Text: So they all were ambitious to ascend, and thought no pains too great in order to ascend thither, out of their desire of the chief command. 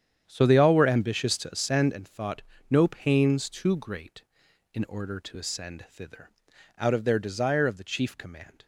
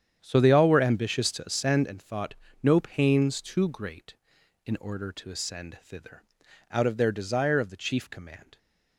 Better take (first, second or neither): neither